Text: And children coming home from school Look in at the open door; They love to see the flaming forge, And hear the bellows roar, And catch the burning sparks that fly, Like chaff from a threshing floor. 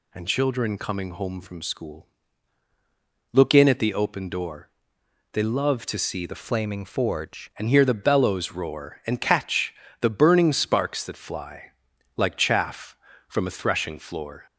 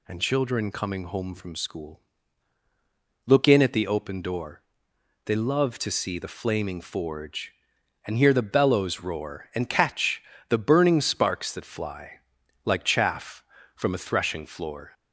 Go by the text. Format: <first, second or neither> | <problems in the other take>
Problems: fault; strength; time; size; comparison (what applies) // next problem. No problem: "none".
second | pauses between "school" and "Look"; at 2.0 s; 1.2 s long; also in the second // changes voice from "flaming" to "forge"; from 6.4 to 7.5 s; 1.1 s long // pauses between "catch" and "the"; slight; at 9.7 s; 0.28 s long; slight in the second